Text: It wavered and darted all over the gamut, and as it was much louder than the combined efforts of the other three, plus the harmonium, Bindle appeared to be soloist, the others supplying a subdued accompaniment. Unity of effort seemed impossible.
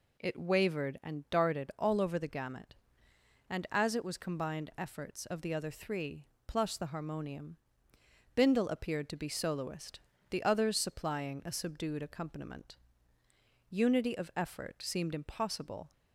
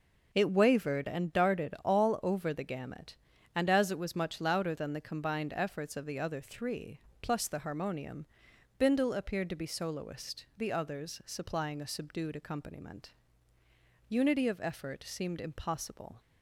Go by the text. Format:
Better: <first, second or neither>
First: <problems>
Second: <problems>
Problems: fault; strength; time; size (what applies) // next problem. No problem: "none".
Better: second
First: skips "much louder than the"; at 4.1 s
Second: none